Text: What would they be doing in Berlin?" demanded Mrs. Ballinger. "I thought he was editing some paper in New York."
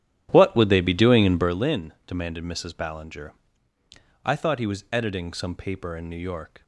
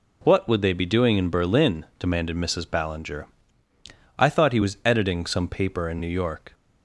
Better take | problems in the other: second | starts louder than the rest; strong; until 1.6 s; 11.5 dB

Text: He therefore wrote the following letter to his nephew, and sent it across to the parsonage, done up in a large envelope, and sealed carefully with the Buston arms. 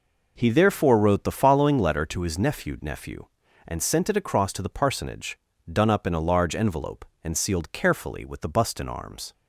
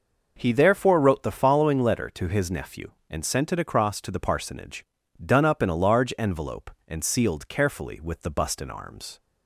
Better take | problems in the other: second | says "nephew" twice; at 2.8 s

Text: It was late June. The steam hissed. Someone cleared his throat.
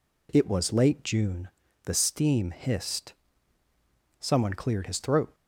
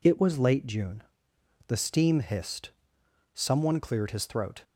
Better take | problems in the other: neither | none

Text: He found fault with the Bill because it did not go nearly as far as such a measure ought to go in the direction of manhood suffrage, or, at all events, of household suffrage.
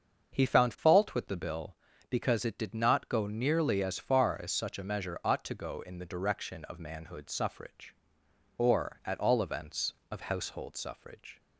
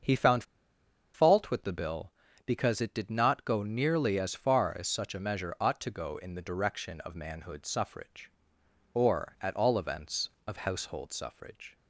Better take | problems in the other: first | starts louder than the rest; until 1.7 s; 6.5 dB; also in the first // pauses between "found" and "fault"; noticeable; at 0.4 s; 0.71 s long

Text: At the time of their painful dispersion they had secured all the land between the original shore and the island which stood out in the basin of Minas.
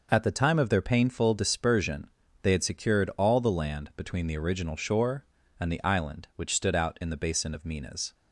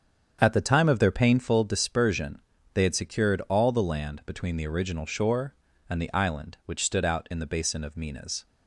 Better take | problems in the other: first | starts louder than the rest; strong; until 1.6 s; 8 dB // pauses between "dispersion" and "they"; slight; at 2.3 s; 0.32 s long; slight in the first

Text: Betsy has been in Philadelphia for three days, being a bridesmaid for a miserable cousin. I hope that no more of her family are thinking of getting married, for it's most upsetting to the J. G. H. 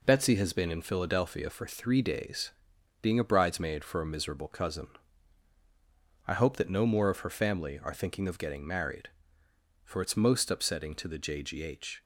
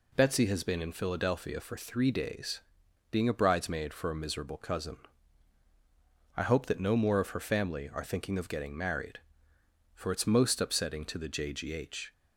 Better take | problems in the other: second | gets quieter; noticeable; throughout; 4.5 dB

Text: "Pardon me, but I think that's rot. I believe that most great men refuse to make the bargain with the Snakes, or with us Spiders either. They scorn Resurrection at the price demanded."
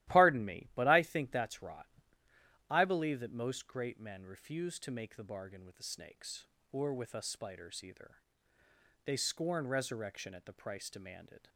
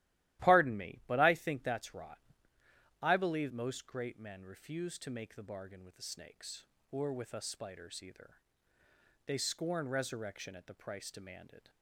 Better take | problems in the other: first | starts louder than the rest; strong; until 1.4 s; 15 dB; strong in the first // skips "that"; at 3.5 s

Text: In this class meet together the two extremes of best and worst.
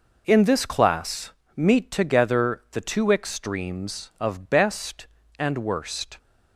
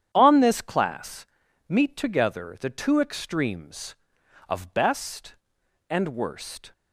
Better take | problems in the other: first | starts louder than the rest; strong; until 1.1 s; 9 dB // says "On" for "In"; at 0.1 s // pauses between "class" and "meet"; at 1.2 s; 0.42 s long; slight in the first

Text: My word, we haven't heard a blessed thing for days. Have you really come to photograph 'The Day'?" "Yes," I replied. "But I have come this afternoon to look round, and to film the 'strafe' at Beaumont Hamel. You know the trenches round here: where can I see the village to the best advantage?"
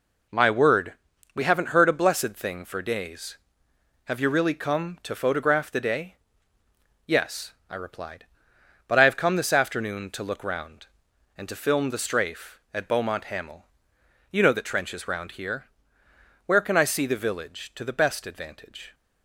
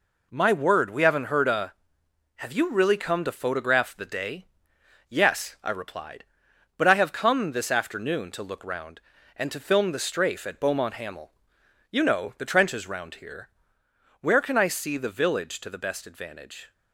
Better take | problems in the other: first | skips "blessed thing for days"; at 2.0 s

